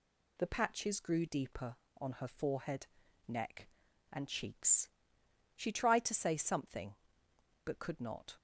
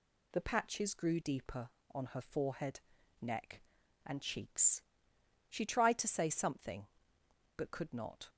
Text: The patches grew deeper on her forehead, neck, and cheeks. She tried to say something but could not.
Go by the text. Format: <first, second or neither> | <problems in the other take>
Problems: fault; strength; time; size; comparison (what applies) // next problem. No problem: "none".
neither | none